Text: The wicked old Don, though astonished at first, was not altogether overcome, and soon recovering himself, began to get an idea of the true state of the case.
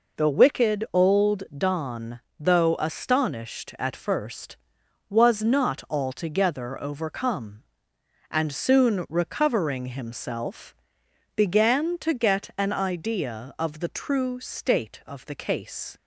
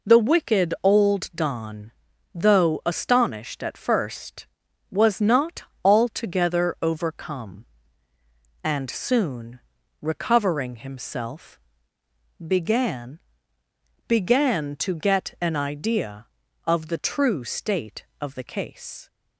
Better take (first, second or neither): first